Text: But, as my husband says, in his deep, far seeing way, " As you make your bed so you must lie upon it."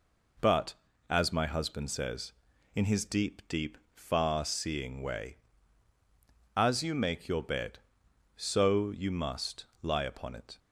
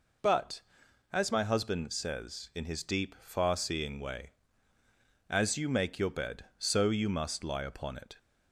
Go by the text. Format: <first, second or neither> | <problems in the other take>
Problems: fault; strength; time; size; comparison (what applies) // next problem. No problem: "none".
second | says "deep" twice; at 3.4 s // pauses between "must" and "lie"; slight; at 9.6 s; 0.18 s long